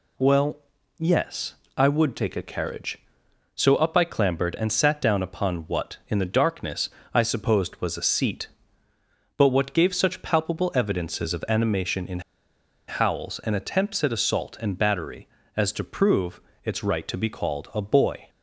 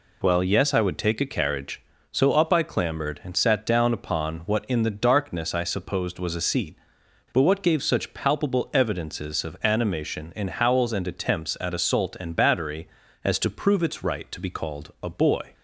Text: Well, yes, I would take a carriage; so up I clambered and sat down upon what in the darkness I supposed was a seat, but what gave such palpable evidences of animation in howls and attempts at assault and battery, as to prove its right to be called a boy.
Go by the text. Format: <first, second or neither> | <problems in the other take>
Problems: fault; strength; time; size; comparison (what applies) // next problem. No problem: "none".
second | pauses between "darkness" and "I"; slight; at 6.8 s; 0.26 s long // pauses between "in" and "howls"; noticeable; at 12.1 s; 0.68 s long // pauses between "prove" and "its"; slight; at 16.4 s; 0.24 s long